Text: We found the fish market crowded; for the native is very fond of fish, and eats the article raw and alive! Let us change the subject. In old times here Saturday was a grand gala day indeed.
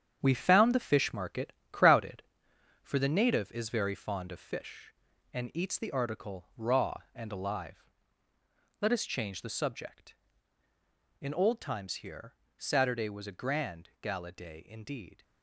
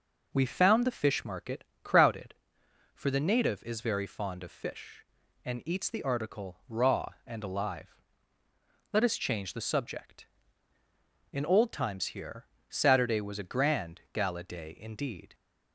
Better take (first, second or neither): second